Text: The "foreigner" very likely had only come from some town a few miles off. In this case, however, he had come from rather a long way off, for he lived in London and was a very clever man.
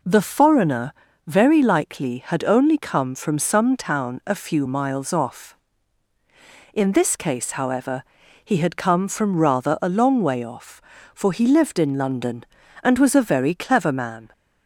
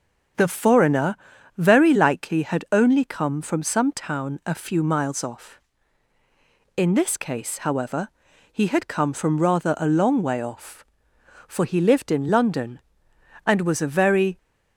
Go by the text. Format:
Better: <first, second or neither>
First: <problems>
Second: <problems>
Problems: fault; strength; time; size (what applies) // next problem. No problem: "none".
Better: first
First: pauses between "foreigner" and "very"; slight; at 0.9 s; 0.34 s long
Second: starts louder than the rest; until 1.7 s; 7 dB // pauses between "foreigner" and "very"; at 1.1 s; 0.40 s long // stops before "clever man"; at 14.3 s